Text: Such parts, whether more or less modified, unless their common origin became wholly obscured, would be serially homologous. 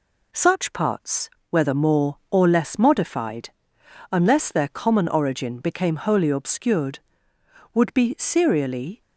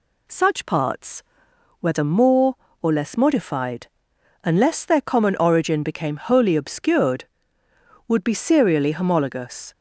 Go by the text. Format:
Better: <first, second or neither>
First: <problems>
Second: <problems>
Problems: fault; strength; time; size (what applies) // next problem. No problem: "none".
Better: second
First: stops before "homologous"; at 9.0 s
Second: none